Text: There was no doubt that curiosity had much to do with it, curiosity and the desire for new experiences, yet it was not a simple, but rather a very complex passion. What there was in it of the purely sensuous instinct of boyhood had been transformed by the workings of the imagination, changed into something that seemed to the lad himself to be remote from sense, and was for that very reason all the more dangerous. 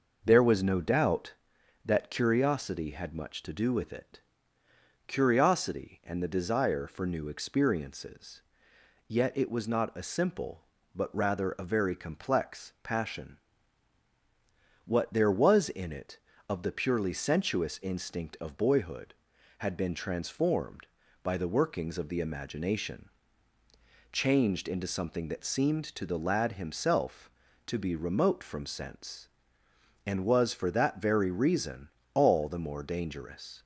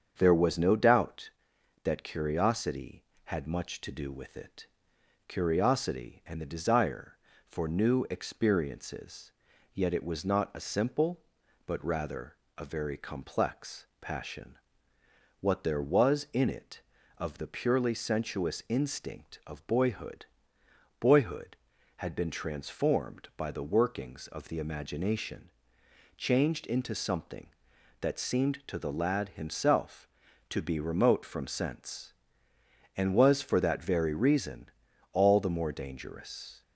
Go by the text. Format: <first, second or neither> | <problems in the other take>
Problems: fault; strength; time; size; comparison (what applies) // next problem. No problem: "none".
first | starts louder than the rest; strong; until 1.1 s; 7.5 dB // pauses between "rather" and "a"; slight; at 12.3 s; 0.20 s long // pauses between "complex" and "passion"; slight; at 13.8 s; 0.16 s long // says "boyhood" twice; at 20.9 s // pauses between "reason" and "all"; at 34.6 s; 0.42 s long; slight in the first